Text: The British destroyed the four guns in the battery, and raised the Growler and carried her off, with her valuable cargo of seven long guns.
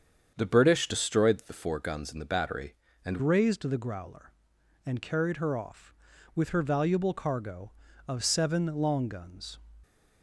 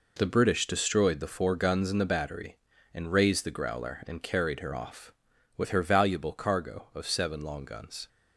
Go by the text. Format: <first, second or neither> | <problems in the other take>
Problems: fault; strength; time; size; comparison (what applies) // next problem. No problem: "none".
second | starts louder than the rest; strong; until 1.3 s; 7.5 dB // changes voice at "raised"; from 3.1 s on; 6.4 s long